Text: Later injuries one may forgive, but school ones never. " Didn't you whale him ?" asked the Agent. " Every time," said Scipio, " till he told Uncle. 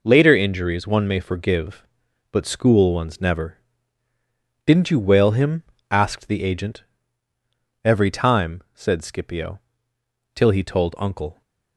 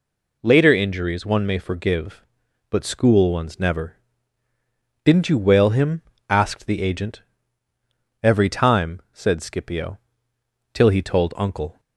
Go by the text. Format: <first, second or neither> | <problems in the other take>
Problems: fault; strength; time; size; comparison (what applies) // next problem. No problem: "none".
second | gets quieter; strong; throughout; 17.5 dB